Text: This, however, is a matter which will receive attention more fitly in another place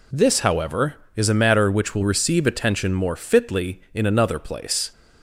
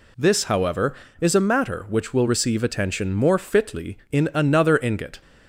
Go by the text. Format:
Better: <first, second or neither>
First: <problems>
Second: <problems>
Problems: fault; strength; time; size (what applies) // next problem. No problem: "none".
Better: first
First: none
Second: says "ingot" for "place"; at 4.8 s